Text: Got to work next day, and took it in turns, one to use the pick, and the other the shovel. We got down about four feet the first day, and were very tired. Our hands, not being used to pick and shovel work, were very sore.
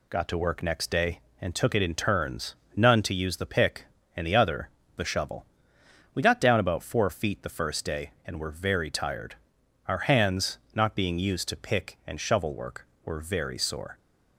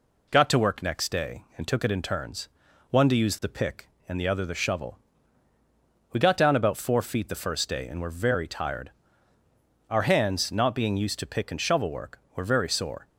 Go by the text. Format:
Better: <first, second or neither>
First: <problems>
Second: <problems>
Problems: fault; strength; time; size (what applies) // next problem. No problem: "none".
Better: second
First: says "none" for "one"; at 2.7 s // pauses between "other" and "the"; slight; at 4.6 s; 0.26 s long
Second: none